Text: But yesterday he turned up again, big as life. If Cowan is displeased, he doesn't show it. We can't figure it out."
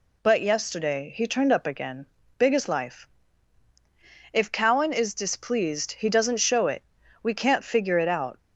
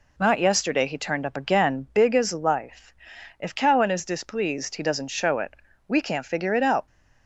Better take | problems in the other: first | says "Not" for "But"; at 0.1 s

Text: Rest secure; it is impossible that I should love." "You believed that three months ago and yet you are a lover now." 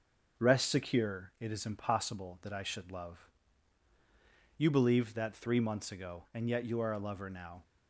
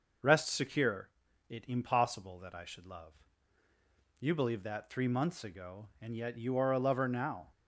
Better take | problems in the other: first | skips "is"; at 1.6 s

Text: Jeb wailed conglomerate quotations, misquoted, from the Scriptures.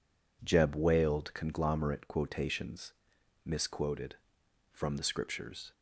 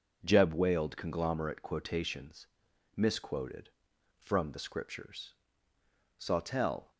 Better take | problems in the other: first | goes on to say "Sawtell"; noticeable; from 6.1 s on; 0.72 s long

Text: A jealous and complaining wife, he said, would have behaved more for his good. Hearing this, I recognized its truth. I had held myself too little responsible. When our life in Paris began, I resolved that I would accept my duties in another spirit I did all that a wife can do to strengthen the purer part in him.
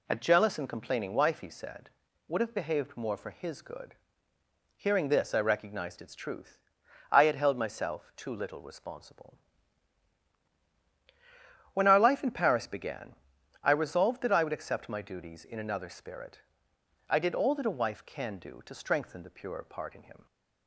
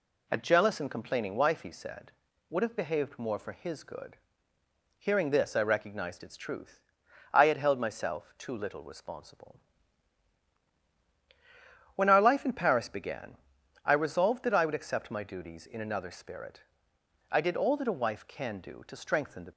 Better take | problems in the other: first | pauses between "spirit" and "I"; noticeable; at 16.6 s; 0.68 s long; noticeable in the first // stops before "purer part in him"; at 19.5 s

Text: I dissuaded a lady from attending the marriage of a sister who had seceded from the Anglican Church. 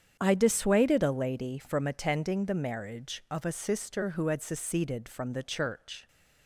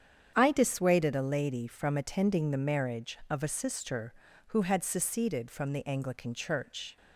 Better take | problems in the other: second | starts louder than the rest; strong; until 1.2 s; 8.5 dB; strong in the second // skips "Anglican"; at 5.4 s

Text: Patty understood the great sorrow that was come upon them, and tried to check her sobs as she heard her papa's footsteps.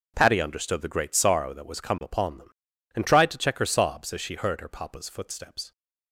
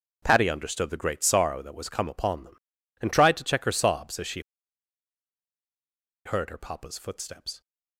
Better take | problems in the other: first | starts louder than the rest; noticeable; until 1.2 s; 6 dB; noticeable in the first // pauses between "she" and "heard"; strong; at 4.3 s; 1.8 s long

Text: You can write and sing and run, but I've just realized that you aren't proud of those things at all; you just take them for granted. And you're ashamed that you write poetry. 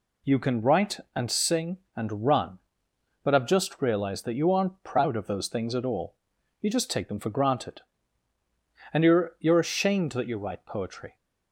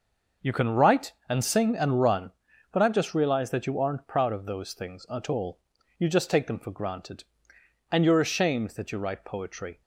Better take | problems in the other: second | says "you're" twice; at 9.3 s

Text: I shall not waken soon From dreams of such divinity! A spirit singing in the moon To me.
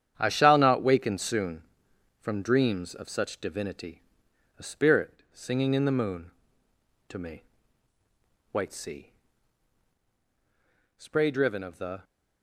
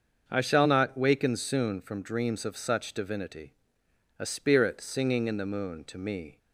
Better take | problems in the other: second | starts louder than the rest; strong; until 1.1 s; 9 dB; also in the second // goes on to say "White sea spray driven of the"; strong; from 8.5 s on; 3.5 s long

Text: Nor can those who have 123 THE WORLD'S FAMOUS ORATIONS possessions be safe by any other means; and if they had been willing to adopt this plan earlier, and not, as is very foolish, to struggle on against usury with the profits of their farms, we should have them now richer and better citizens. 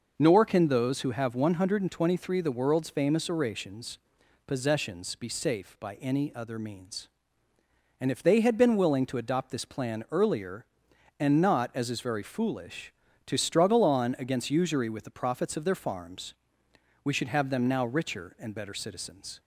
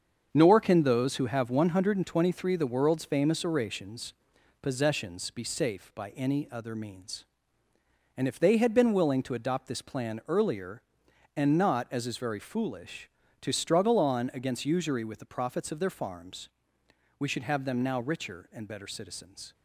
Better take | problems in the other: first | gets quieter; strong; throughout; 8.5 dB // pauses between "ORATIONS" and "possessions"; noticeable; at 4.1 s; 0.48 s long; noticeable in the first

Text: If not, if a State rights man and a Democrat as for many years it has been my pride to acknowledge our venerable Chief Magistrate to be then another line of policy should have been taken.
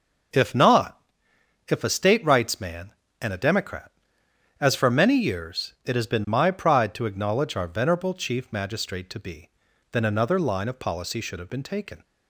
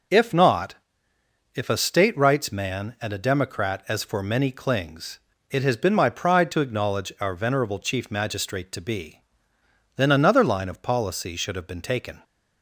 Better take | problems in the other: first | says "clings" for "years"; at 4.5 s // pauses between "be" and "then"; noticeable; at 9.2 s; 0.74 s long; also in the first

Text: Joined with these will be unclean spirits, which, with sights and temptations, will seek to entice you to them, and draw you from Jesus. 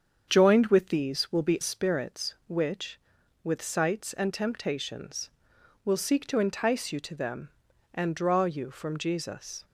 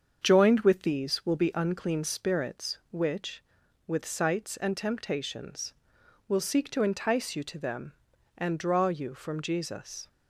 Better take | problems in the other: second | starts louder than the rest; strong; until 1.2 s; 7.5 dB; also in the second // skips "unclean"; at 1.5 s

